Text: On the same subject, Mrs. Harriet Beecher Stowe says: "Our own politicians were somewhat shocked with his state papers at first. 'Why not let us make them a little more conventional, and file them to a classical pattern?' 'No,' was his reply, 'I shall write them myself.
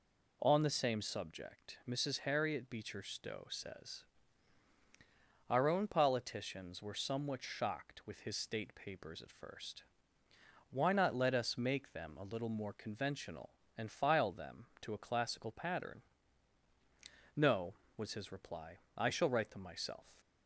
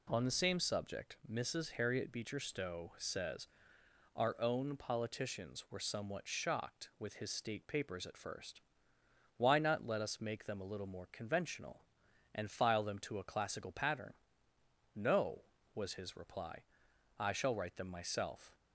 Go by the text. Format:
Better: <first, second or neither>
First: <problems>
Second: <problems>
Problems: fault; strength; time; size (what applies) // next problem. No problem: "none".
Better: neither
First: none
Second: none